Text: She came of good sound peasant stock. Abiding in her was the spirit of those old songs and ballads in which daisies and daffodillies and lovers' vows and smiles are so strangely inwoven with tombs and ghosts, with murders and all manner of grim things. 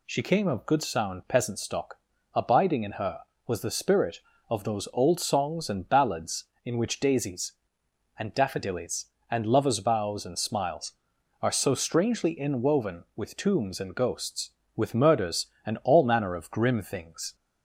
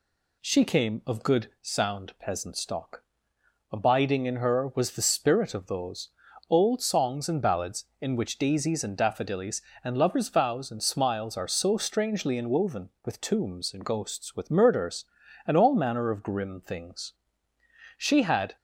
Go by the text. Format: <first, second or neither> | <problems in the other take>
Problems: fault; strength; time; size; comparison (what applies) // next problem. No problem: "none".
first | pauses between "those" and "old"; at 6.0 s; 0.38 s long // goes on to say "She had"; from 17.9 s on; 0.58 s long